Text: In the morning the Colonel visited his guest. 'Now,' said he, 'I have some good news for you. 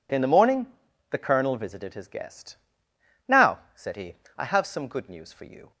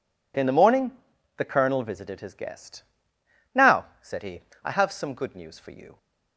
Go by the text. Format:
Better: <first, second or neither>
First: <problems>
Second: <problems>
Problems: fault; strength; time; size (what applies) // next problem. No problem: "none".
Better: neither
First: pauses between "morning" and "the"; at 0.6 s; 0.44 s long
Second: pauses between "morning" and "the"; noticeable; at 0.9 s; 0.46 s long